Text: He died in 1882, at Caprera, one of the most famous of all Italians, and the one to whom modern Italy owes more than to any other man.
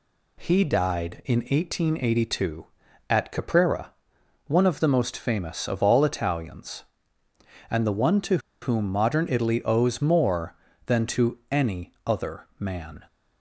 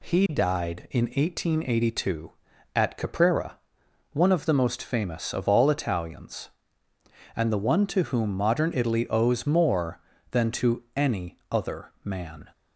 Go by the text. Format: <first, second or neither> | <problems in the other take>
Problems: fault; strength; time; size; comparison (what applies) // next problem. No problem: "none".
second | pauses between "to" and "whom"; slight; at 8.3 s; 0.24 s long